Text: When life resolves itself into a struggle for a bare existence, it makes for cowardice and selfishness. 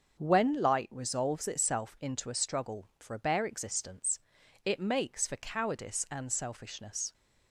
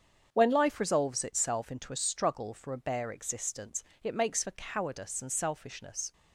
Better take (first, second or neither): second